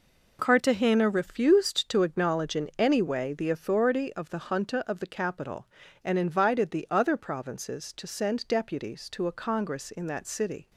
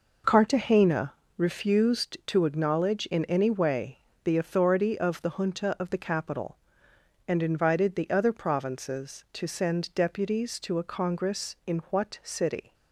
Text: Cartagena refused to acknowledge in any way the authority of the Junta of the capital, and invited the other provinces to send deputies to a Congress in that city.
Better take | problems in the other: first | pauses between "Cartagena" and "refused"; slight; at 1.1 s; 0.24 s long // pauses between "way" and "the"; slight; at 3.9 s; 0.24 s long // says "what" for "that"; at 11.9 s

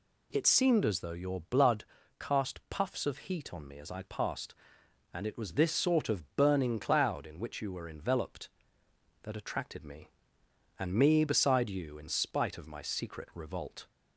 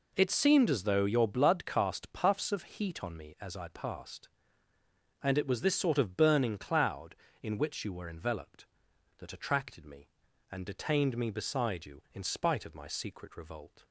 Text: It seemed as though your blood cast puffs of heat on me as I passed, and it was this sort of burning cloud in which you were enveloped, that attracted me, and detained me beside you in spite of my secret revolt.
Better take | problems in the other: second | pauses between "blood" and "cast"; slight; at 1.8 s; 0.36 s long // skips "detained"; at 10.9 s

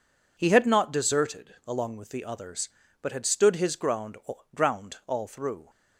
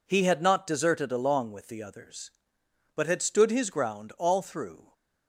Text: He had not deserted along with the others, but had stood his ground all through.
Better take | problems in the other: second | says "ground" twice; at 4.5 s

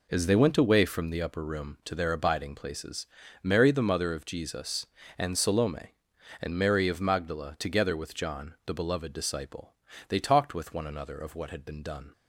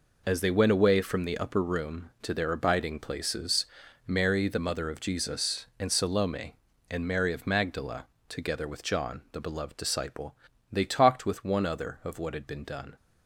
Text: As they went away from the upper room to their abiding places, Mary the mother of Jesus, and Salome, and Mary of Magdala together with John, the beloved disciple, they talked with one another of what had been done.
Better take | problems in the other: first | pauses between "Magdala" and "together"; slight; at 8.0 s; 0.24 s long // says "other" for "another"; at 11.6 s

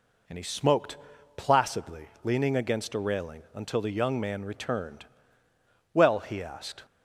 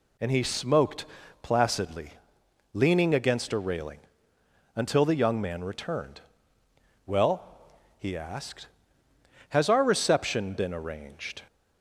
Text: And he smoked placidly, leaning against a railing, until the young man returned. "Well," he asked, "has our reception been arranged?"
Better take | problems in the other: second | pauses between "smoked" and "placidly"; at 0.9 s; 0.39 s long; slight in the second // stops before "has our reception been arranged"; at 6.8 s

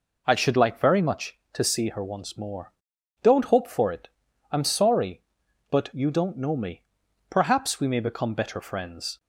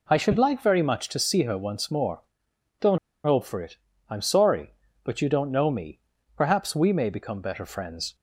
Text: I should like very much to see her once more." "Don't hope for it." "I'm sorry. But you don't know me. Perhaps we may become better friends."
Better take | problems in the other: first | pauses between "Don't" and "hope"; slight; at 2.9 s; 0.26 s long

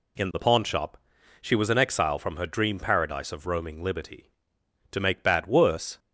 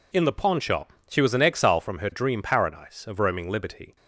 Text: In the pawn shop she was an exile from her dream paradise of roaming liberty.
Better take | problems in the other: second | pauses between "shop" and "she"; at 0.9 s; 0.44 s long; slight in the second // goes on to say "To make bad worse"; noticeable; from 4.9 s on; 1.0 s long

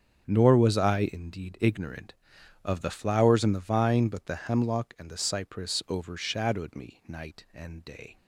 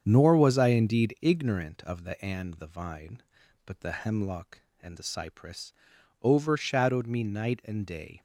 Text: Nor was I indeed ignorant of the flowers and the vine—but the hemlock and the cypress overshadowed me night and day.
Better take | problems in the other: first | starts louder than the rest; strong; until 1.0 s; 7.5 dB; strong in the first // skips "flowers"; at 2.2 s // pauses between "cypress" and "overshadowed"; noticeable; at 5.7 s; 0.50 s long

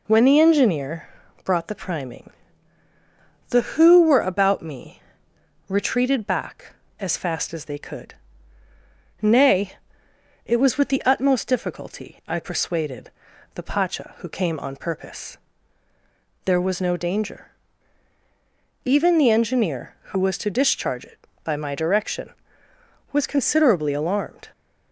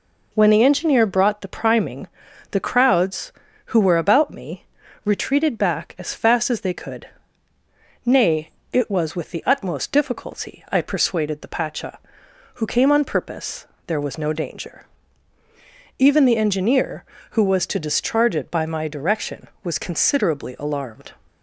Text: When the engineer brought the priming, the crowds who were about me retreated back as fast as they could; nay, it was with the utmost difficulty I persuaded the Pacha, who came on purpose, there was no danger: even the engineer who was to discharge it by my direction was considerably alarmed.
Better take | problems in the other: second | pauses between "engineer" and "brought"; slight; at 1.0 s; 0.34 s long // skips "crowds"; at 3.6 s // pauses between "me" and "retreated"; noticeable; at 5.0 s; 0.68 s long; also in the second // pauses between "persuaded" and "the"; at 13.1 s; 0.44 s long

